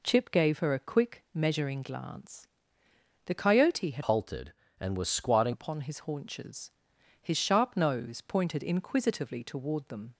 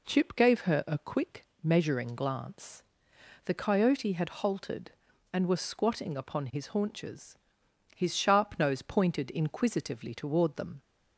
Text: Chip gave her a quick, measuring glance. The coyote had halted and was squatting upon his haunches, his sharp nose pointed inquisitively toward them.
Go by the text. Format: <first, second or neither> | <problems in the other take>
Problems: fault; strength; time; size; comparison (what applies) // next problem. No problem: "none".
second | changes voice from "halted" to "squatting"; from 4.0 to 5.5 s; 1.5 s long